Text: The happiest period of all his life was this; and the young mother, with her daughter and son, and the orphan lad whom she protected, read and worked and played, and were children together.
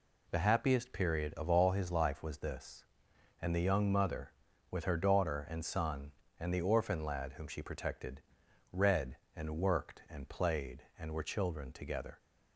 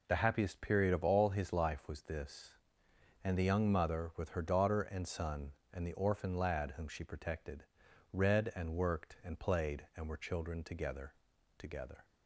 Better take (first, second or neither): first